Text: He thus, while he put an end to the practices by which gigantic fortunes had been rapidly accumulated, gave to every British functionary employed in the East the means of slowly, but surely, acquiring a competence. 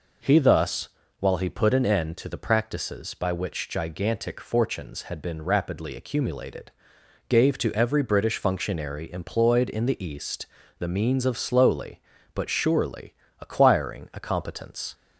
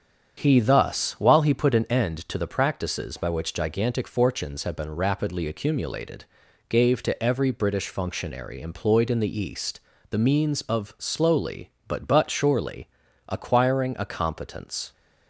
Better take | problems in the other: first | starts louder than the rest; strong; until 1.3 s; 8 dB // pauses between "East" and "the"; slight; at 9.8 s; 0.30 s long; slight in the first // says "but" twice; at 12.0 s

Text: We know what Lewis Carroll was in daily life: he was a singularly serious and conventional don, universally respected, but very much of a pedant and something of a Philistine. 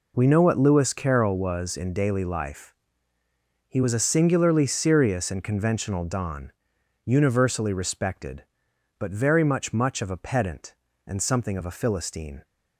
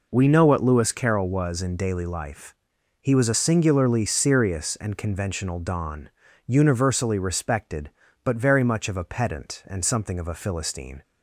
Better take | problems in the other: second | says "much" twice; at 9.7 s

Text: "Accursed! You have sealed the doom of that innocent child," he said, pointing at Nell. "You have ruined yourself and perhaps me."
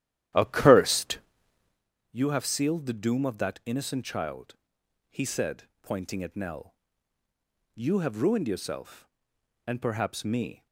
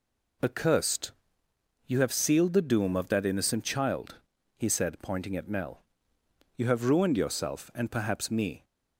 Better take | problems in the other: second | starts louder than the rest; strong; until 1.9 s; 12 dB

